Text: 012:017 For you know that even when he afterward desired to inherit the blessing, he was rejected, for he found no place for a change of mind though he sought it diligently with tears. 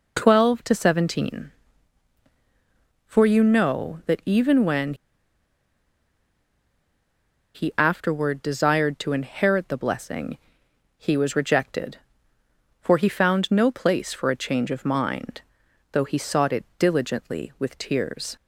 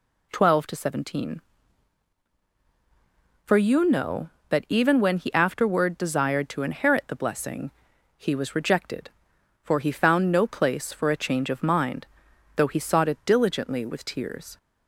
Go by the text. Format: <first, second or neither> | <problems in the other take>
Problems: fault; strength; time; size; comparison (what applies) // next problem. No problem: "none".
second | pauses between "when" and "he"; strong; at 4.9 s; 2.6 s long // pauses between "mind" and "though"; noticeable; at 15.3 s; 0.54 s long; noticeable in the second